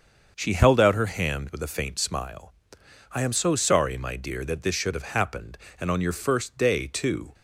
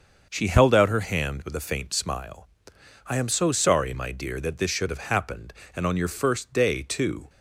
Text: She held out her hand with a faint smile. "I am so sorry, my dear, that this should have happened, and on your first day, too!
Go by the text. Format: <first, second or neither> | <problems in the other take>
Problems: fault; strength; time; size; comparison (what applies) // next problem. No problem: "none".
neither | starts louder than the rest; the same in both